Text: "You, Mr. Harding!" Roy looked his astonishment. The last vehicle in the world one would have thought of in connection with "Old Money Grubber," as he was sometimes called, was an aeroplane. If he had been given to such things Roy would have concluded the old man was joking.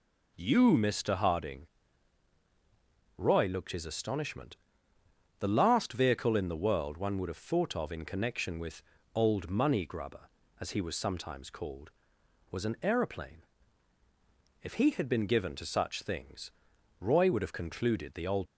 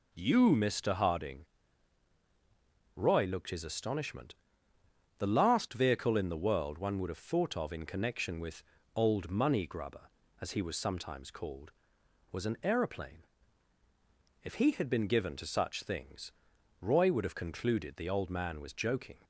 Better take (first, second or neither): second